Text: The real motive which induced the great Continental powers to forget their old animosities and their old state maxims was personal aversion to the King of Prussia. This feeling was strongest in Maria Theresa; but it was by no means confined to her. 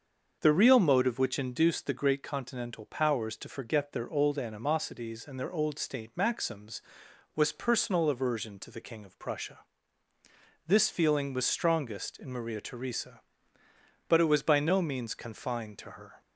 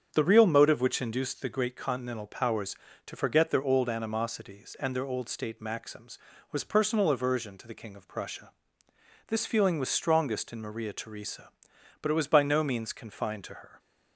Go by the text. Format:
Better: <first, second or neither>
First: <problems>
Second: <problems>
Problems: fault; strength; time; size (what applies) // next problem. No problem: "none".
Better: neither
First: starts louder than the rest; until 1.4 s; 6.5 dB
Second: starts louder than the rest; strong; until 1.1 s; 7.5 dB